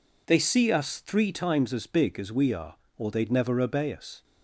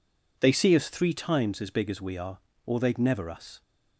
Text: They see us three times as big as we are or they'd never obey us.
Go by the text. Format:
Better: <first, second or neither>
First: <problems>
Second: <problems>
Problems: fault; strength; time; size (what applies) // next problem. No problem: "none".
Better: first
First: none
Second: skips "obey"; at 3.2 s